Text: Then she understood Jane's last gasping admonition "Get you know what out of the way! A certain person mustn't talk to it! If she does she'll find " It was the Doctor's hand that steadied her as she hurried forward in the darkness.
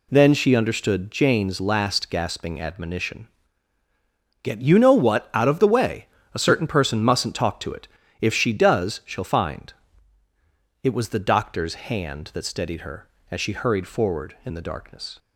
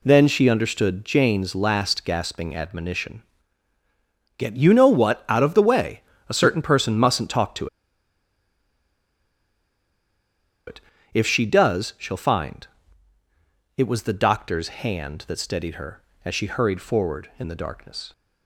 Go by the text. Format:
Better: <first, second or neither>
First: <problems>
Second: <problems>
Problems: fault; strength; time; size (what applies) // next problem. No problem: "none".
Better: first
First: pauses between "admonition" and "Get"; at 3.2 s; 1.1 s long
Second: pauses between "admonition" and "Get"; at 3.2 s; 1.1 s long // pauses between "to" and "it"; strong; at 7.6 s; 2.9 s long